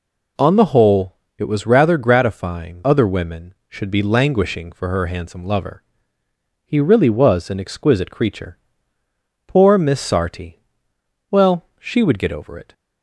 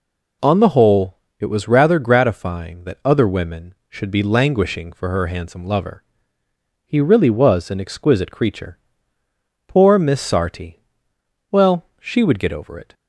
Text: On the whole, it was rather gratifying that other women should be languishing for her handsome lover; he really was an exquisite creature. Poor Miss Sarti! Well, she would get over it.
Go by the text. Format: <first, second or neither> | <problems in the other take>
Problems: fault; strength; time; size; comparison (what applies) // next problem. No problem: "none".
second | skips "that"; at 2.8 s